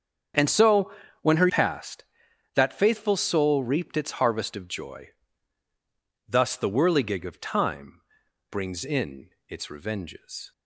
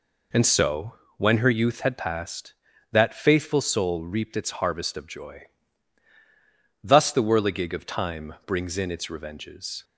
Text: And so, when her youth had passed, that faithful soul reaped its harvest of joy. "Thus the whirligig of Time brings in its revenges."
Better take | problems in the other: second | starts louder than the rest; strong; until 1.6 s; 7.5 dB // skips "youth had"; at 1.4 s // pauses between "Time" and "brings"; noticeable; at 8.0 s; 0.48 s long // pauses between "in" and "its"; slight; at 9.2 s; 0.18 s long

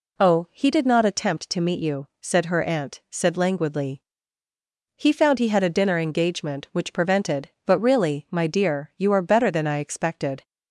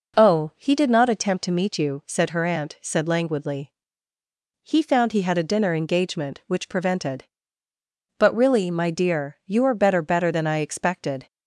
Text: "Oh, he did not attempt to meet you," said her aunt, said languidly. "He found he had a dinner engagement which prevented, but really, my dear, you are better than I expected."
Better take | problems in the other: first | says "better" twice; at 10.0 s

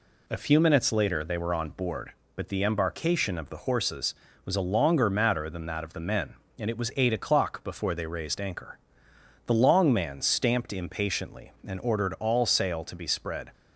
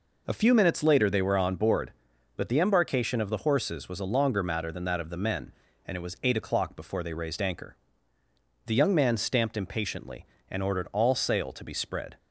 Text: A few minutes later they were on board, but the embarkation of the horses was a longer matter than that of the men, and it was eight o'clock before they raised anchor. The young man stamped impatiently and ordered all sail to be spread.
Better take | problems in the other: second | says "long" for "young"; at 9.5 s

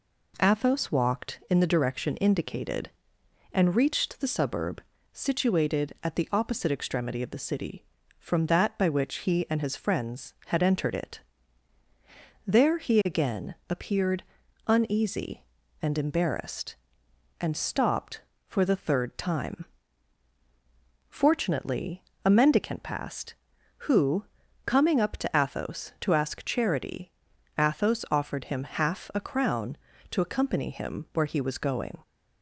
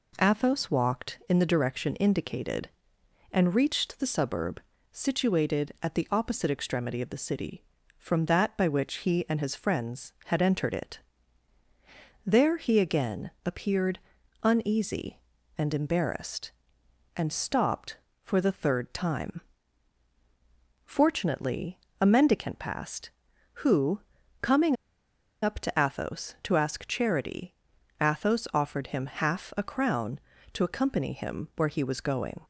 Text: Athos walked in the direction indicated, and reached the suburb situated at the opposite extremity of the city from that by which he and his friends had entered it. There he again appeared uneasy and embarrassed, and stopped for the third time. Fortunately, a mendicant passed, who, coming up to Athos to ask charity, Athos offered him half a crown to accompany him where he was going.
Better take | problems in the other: first | pauses between "suburb" and "situated"; slight; at 4.5 s; 0.32 s long; slight in the first // pauses between "again" and "appeared"; slight; at 13.2 s; 0.16 s long; slight in the first // pauses between "appeared" and "uneasy"; at 13.9 s; 0.44 s long; also in the first // pauses between "coming" and "up"; noticeable; at 24.7 s; 0.67 s long

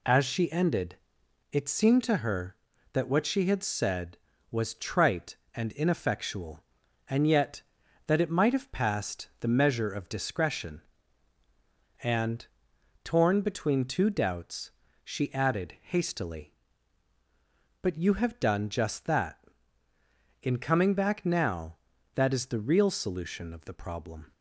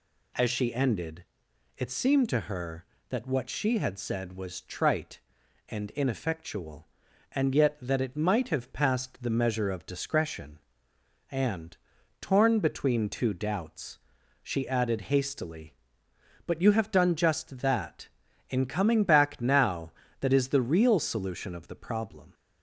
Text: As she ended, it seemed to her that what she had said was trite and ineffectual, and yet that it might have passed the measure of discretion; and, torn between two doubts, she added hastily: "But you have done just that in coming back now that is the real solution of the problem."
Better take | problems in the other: neither | none

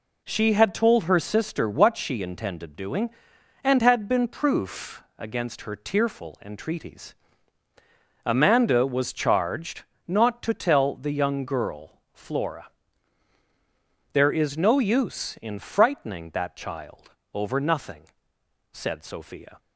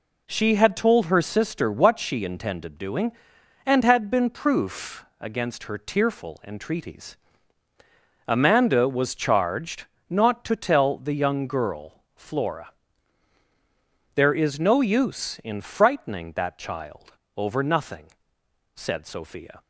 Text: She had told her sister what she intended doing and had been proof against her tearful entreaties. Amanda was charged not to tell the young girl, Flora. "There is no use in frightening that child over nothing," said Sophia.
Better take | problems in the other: neither | pauses between "charged" and "not"; slight; the same in both // pauses between "child" and "over"; slight; the same in both

